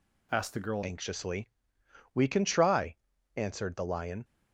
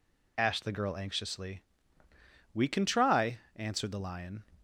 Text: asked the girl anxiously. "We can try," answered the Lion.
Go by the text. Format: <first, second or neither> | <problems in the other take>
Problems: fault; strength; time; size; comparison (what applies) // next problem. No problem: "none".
second | changes voice at "anxiously"; from 0.8 s on; 3.4 s long